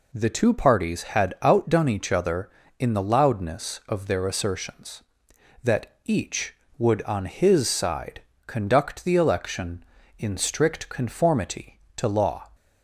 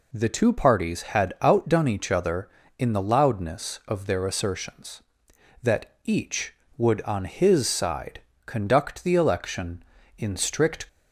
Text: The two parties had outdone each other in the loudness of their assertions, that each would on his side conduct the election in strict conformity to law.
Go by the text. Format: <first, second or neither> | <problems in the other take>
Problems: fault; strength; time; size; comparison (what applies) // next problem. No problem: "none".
first | pauses between "side" and "conduct"; slight; at 8.2 s; 0.26 s long; slight in the first // stops before "conformity to law"; at 10.8 s